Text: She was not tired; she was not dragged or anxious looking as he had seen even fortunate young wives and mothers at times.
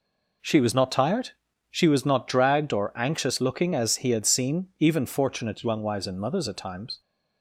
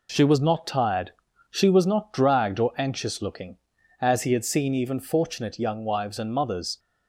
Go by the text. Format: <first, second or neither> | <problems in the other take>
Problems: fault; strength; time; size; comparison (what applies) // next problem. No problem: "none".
first | stops before "at times"; at 6.7 s